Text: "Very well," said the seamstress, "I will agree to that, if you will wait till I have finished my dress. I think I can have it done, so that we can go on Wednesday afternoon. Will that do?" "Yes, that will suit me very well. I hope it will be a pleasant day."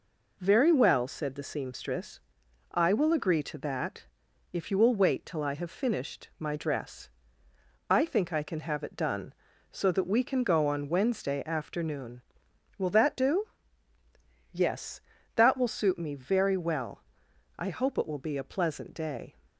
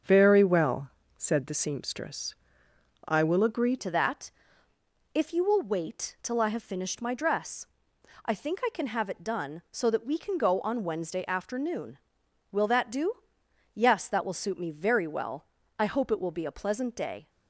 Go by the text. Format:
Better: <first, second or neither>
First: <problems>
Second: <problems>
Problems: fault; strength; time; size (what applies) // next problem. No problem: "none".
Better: first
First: none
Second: starts louder than the rest; until 1.3 s; 6.5 dB // changes voice at "to"; from 3.7 s on; 13.5 s long